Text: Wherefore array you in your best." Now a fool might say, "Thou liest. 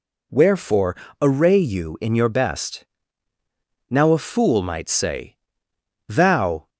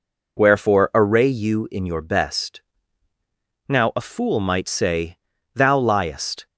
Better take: second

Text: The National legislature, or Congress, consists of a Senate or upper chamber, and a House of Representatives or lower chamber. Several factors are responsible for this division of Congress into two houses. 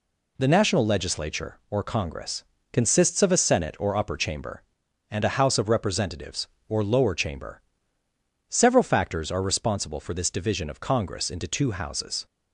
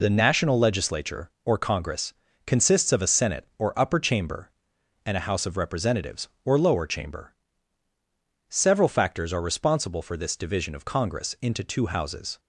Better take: neither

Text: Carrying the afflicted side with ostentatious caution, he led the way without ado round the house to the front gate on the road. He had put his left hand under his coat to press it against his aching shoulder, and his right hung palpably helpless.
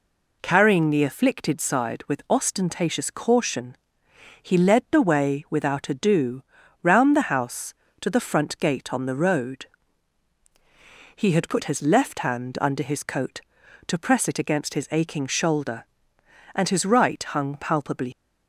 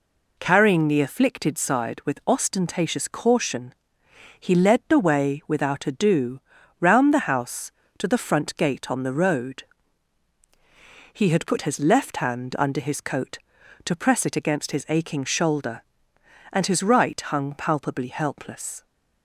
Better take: second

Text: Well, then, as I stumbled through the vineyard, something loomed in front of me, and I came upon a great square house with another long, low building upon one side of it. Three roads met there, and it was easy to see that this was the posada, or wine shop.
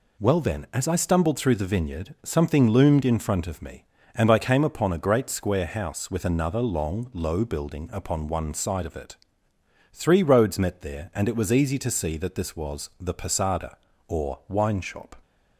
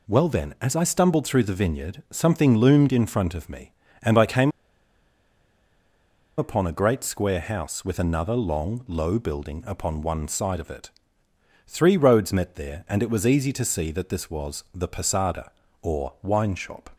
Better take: first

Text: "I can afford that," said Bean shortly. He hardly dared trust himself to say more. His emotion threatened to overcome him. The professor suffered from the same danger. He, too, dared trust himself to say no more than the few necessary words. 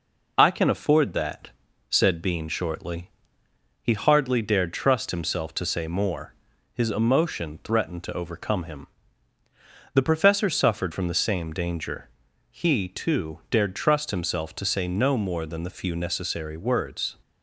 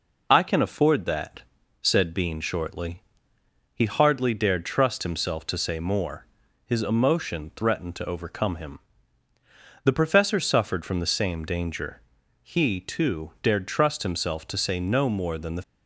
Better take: first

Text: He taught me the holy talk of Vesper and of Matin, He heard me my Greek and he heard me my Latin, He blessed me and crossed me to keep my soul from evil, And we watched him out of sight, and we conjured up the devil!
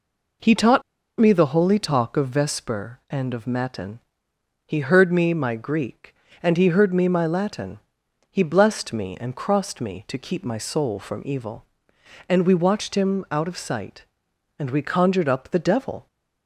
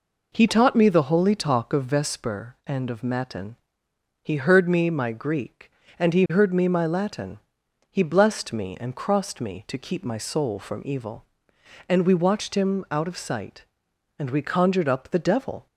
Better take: second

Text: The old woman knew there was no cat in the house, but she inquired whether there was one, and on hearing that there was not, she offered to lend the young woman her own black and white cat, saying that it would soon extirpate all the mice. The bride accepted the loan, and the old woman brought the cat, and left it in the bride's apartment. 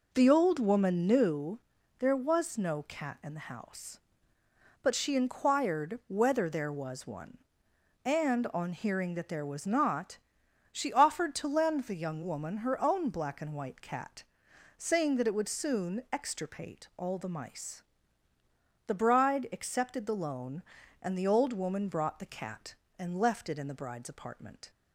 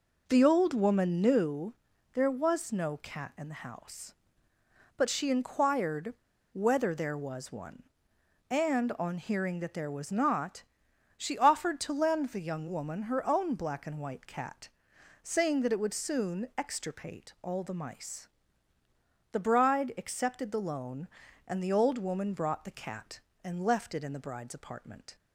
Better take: first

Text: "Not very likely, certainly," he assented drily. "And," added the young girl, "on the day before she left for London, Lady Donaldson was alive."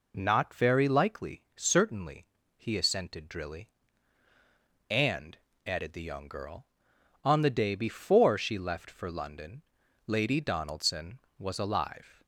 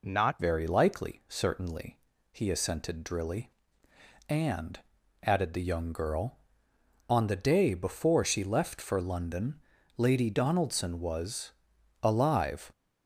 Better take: first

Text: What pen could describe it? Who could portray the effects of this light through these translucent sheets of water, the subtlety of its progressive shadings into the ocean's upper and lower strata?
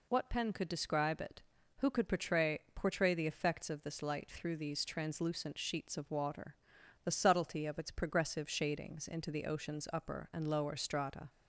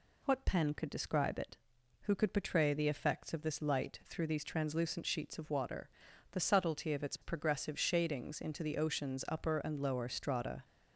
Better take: second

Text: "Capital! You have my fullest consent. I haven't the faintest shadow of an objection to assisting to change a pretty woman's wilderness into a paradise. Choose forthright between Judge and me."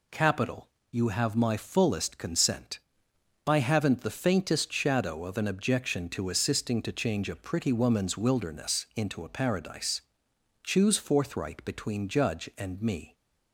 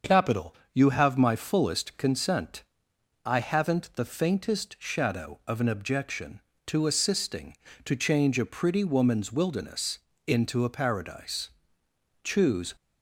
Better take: first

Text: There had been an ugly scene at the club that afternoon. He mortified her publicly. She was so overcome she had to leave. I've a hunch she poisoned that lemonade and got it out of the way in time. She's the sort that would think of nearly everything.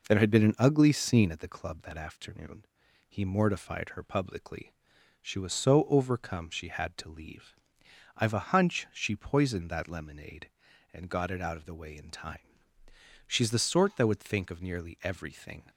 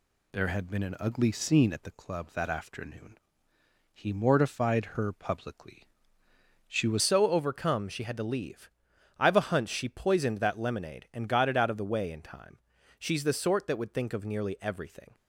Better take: first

